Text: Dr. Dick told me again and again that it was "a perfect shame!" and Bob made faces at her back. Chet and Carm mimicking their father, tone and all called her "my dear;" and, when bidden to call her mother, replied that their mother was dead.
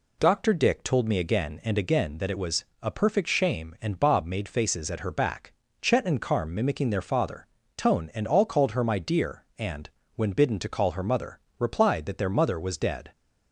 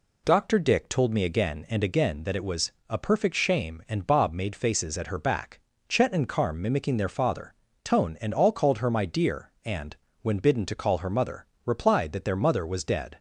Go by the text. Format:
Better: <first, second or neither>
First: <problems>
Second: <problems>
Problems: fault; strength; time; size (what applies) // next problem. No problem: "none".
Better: neither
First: pauses between "was" and "a"; slight; at 2.6 s; 0.18 s long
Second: pauses between "was" and "a"; slight; at 2.7 s; 0.18 s long